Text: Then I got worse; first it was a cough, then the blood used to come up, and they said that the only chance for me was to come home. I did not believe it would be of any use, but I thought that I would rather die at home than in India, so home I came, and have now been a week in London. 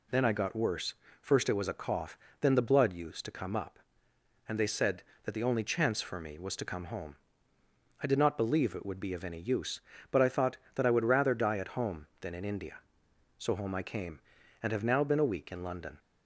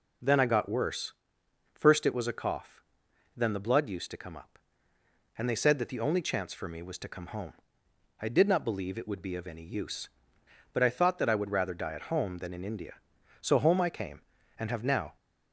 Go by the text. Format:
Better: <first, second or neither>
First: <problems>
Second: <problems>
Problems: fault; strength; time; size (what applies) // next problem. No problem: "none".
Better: first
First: none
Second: stops before "been a week in London"; at 15.1 s